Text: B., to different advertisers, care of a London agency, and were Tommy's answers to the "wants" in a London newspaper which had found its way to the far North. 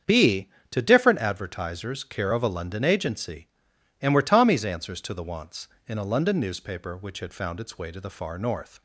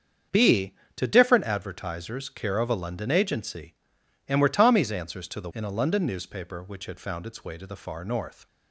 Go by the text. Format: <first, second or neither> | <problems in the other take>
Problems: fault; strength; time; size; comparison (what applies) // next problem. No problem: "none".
first | starts louder than the rest; strong; until 1.5 s; 7.5 dB; strong in the first // skips "wants"; at 5.5 s